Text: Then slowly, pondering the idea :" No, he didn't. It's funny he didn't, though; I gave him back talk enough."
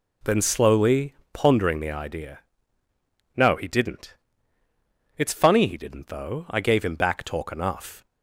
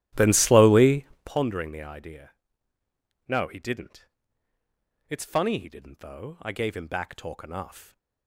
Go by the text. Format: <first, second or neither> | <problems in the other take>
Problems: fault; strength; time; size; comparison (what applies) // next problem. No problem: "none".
first | starts louder than the rest; strong; until 1.3 s; 13.5 dB